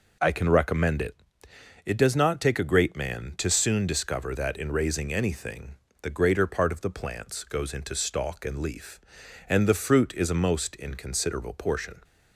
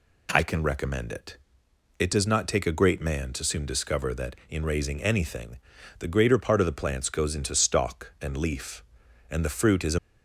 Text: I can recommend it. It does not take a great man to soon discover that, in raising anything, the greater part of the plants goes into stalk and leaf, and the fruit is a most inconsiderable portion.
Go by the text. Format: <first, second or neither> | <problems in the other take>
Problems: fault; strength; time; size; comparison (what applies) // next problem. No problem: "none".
first | stops before "most inconsiderable portion"; at 9.9 s